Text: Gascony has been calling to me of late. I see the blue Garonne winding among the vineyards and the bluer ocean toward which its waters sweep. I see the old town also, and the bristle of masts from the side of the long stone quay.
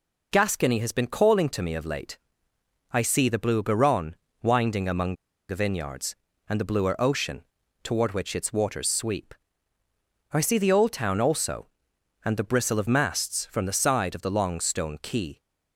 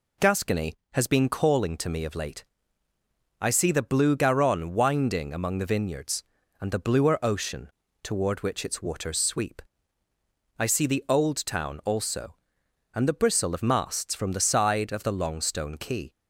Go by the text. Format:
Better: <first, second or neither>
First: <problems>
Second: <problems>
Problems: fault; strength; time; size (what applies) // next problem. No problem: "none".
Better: second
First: pauses between "Garonne" and "winding"; slight; at 4.1 s; 0.26 s long // pauses between "among" and "the"; at 5.1 s; 0.36 s long // pauses between "ocean" and "toward"; at 7.4 s; 0.40 s long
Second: pauses between "ocean" and "toward"; slight; at 7.7 s; 0.32 s long